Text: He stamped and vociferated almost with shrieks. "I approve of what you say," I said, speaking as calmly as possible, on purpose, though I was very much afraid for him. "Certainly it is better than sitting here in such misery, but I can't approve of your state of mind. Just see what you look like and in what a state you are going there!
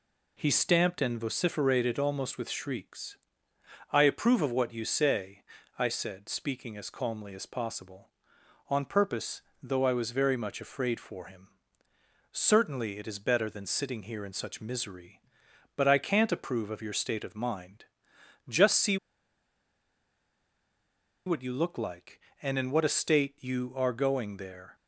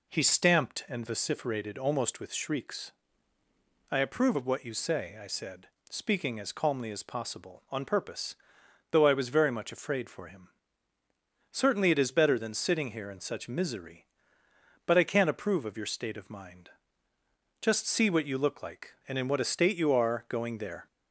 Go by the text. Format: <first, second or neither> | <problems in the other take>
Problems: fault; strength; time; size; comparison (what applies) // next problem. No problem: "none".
second | pauses between "see" and "what"; strong; at 18.9 s; 2.3 s long